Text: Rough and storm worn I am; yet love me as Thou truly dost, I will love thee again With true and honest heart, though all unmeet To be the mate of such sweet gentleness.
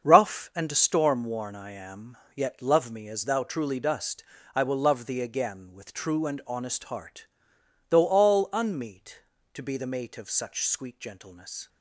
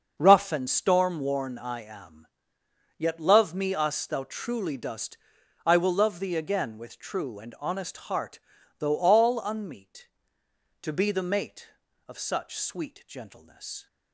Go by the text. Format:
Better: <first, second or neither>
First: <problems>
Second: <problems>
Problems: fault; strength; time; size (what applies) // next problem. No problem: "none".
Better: first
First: starts louder than the rest; until 1.0 s; 7 dB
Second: starts louder than the rest; until 1.1 s; 6.5 dB // says "us" for "as"; at 3.7 s